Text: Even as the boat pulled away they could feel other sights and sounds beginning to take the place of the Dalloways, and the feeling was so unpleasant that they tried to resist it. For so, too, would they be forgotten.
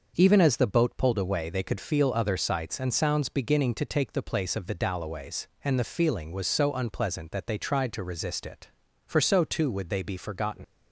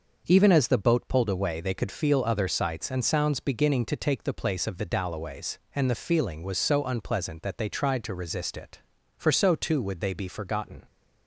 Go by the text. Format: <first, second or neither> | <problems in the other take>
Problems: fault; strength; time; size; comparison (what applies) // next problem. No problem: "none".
second | leaves "forgotten" unfinished; at 10.6 s; 100 ms